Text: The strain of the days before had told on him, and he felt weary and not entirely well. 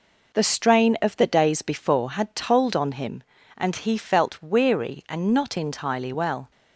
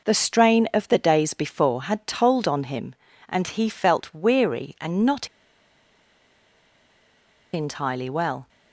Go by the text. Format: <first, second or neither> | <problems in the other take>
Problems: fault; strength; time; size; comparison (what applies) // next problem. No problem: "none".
first | pauses between "not" and "entirely"; strong; at 5.2 s; 2.2 s long